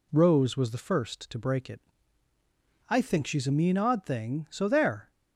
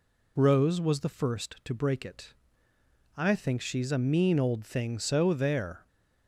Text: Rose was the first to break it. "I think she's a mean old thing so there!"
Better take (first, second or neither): second